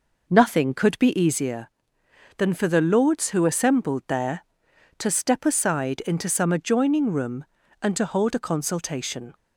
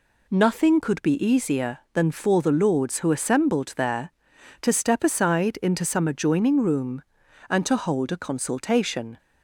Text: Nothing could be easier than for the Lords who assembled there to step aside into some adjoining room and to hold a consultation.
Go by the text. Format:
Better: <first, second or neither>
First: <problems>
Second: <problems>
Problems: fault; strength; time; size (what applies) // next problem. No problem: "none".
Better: second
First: starts louder than the rest; noticeable; until 1.5 s; 5 dB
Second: none